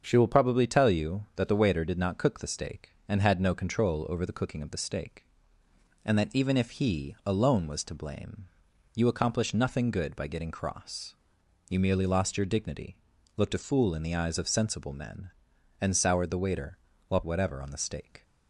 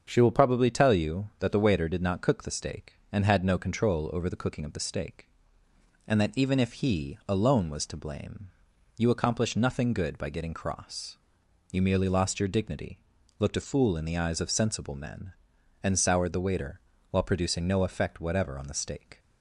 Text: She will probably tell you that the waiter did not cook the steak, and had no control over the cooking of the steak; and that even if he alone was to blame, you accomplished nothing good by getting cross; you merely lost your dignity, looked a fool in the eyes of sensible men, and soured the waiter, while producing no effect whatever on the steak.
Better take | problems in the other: second | starts louder than the rest; until 1.0 s; 7 dB; also in the second // skips "producing no effect"; at 17.2 s

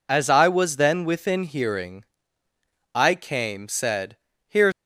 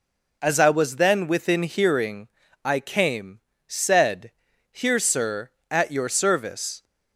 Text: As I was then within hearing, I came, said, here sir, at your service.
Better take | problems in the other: second | stops before "sir at your service"; at 4.7 s

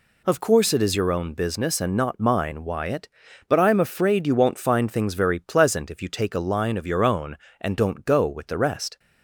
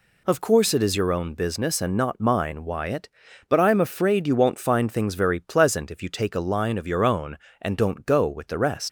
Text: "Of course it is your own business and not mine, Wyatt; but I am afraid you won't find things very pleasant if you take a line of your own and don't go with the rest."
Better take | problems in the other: first | leaves "rest" unfinished; at 8.8 s; 95 ms

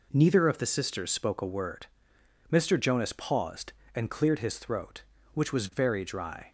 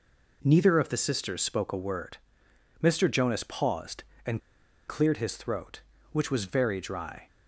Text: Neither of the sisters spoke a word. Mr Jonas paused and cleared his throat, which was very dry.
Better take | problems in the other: first | pauses between "and" and "cleared"; noticeable; at 4.3 s; 0.48 s long

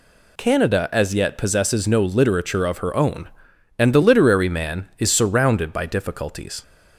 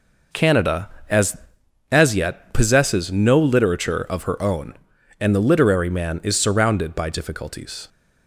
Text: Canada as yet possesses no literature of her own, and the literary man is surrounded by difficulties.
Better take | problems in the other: first | says "as" twice; at 1.8 s

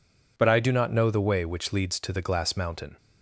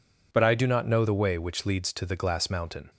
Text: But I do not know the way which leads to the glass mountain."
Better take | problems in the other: neither | none

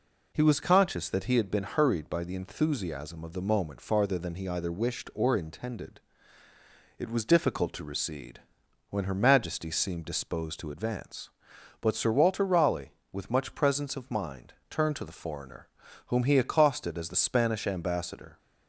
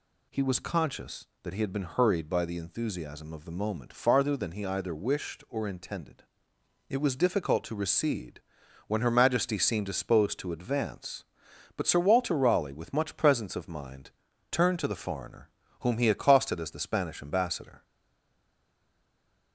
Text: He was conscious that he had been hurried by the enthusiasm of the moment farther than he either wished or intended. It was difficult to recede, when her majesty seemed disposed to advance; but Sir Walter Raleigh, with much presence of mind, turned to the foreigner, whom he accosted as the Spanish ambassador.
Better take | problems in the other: first | stays silent after the last word; noticeable; from 17.8 s on; 1.7 s long

